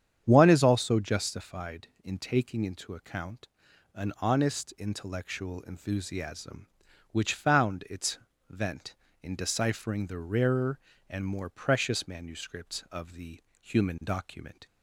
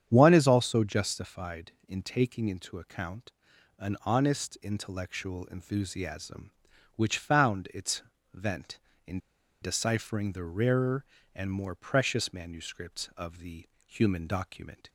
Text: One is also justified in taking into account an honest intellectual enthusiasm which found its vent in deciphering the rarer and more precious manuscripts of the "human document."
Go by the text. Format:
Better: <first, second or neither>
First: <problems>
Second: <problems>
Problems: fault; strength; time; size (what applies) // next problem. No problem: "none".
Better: first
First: starts louder than the rest; strong; until 1.2 s; 8.5 dB // pauses between "account" and "an"; noticeable; at 3.4 s; 0.48 s long // pauses between "its" and "vent"; slight; at 8.1 s; 0.30 s long // pauses between "the" and "human"; slight; at 13.4 s; 0.18 s long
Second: starts louder than the rest; strong; until 1.1 s; 8.5 dB // pauses between "account" and "an"; noticeable; at 3.3 s; 0.48 s long // pauses between "its" and "vent"; slight; at 8.0 s; 0.30 s long // pauses between "in" and "deciphering"; at 9.1 s; 0.44 s long // pauses between "the" and "human"; slight; at 13.6 s; 0.18 s long